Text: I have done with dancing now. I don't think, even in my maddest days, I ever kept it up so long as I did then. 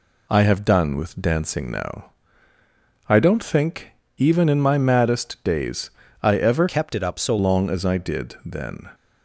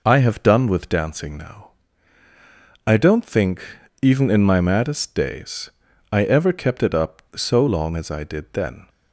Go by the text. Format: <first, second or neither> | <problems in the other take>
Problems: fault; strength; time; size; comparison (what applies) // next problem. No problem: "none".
second | changes voice from "kept" to "so"; from 6.6 to 7.3 s; 0.7 s long